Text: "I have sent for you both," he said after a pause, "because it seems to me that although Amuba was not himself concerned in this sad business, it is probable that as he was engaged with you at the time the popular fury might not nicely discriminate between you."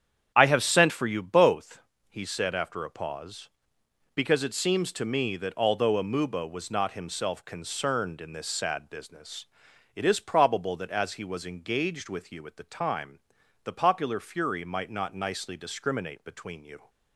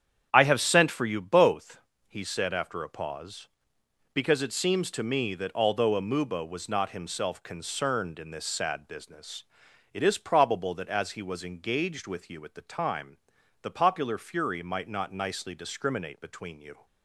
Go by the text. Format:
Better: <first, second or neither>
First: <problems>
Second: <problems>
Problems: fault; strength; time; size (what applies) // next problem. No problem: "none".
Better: neither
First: starts louder than the rest; strong; until 1.3 s; 8.5 dB // pauses between "time" and "the"; at 13.1 s; 0.44 s long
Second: starts louder than the rest; strong; until 1.3 s; 8.5 dB // pauses between "time" and "the"; at 13.1 s; 0.44 s long